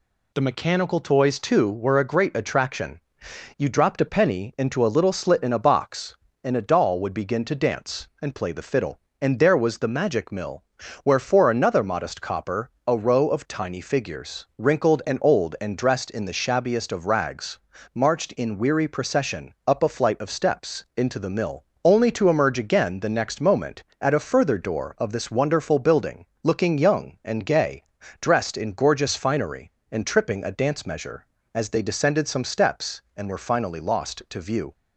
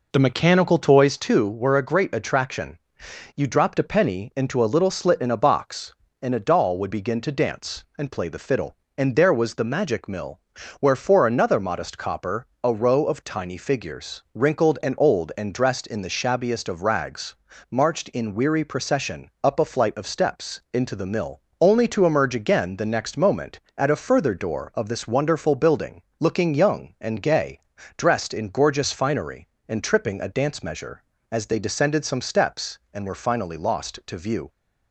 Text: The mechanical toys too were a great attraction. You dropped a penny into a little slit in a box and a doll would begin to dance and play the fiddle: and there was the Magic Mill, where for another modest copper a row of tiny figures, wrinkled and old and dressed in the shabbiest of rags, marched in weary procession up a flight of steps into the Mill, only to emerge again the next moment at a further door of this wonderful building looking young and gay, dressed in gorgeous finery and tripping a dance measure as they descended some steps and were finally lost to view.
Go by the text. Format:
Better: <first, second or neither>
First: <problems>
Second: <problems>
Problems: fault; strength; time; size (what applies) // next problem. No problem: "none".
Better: first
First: pauses between "copper" and "a"; slight; at 12.7 s; 0.16 s long // pauses between "building" and "looking"; slight; at 26.2 s; 0.18 s long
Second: starts louder than the rest; noticeable; until 1.2 s; 4.5 dB // pauses between "copper" and "a"; slight; at 12.4 s; 0.16 s long // pauses between "building" and "looking"; slight; at 26.0 s; 0.18 s long